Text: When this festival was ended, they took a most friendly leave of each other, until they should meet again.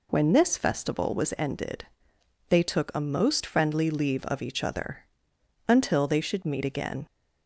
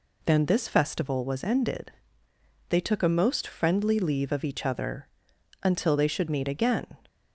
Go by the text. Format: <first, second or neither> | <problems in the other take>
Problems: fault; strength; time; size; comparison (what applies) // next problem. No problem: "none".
first | says "Then" for "When"; at 0.2 s